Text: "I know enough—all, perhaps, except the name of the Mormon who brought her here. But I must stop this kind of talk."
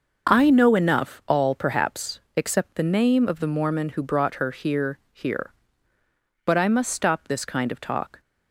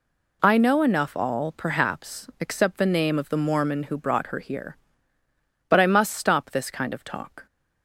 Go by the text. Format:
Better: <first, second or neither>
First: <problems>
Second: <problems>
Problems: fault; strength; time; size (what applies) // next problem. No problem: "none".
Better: second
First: says "here" twice; at 5.1 s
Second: none